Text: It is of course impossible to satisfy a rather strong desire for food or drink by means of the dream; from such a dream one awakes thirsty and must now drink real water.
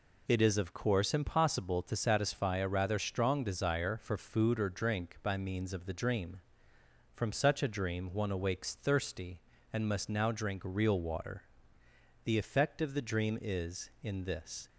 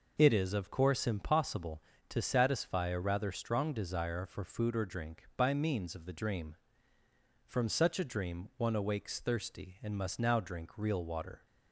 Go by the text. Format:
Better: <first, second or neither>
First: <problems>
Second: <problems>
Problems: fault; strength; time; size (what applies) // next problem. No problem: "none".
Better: second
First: goes on to say "The effect of the dream is in this"; strong; from 12.2 s on; 2.4 s long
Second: none